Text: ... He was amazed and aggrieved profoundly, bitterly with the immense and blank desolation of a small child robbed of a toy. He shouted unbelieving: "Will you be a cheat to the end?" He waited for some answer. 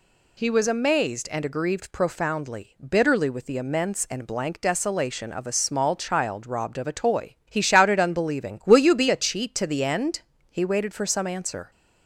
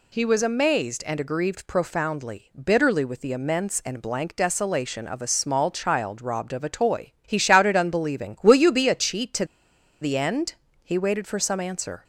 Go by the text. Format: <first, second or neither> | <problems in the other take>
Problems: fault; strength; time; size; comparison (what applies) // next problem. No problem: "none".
first | pauses between "to" and "the"; noticeable; at 9.4 s; 0.56 s long